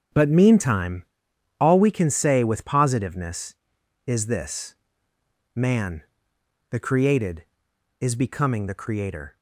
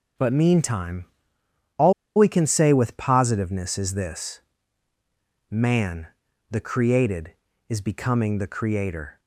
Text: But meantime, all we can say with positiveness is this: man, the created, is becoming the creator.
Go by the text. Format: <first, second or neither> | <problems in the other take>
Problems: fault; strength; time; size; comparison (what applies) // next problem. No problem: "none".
first | starts louder than the rest; until 1.9 s; 6.5 dB; strong in the first // pauses between "all" and "we"; slight; at 1.9 s; 0.23 s long